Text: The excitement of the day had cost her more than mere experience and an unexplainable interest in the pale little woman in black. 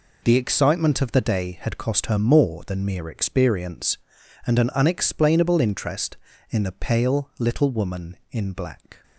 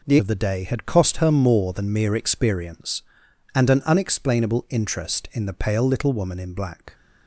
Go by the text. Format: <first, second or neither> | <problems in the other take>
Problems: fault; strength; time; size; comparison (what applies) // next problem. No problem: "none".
first | skips "excitement"; at 0.1 s